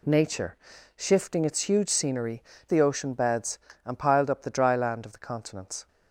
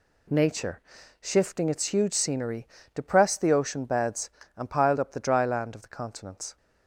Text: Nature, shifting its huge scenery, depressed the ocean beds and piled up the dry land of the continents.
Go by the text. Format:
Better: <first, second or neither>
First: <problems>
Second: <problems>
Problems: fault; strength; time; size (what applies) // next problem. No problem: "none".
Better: second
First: skips "depressed"; at 2.5 s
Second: none